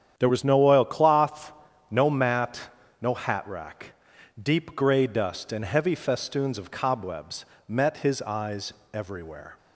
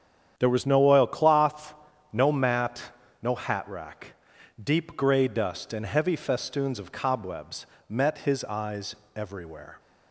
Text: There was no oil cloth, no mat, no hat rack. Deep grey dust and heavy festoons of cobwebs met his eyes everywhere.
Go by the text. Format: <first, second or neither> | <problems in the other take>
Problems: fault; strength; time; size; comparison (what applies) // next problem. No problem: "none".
neither | starts louder than the rest; strong; the same in both // pauses between "cobwebs" and "met"; slight; the same in both // pauses between "eyes" and "everywhere"; slight; the same in both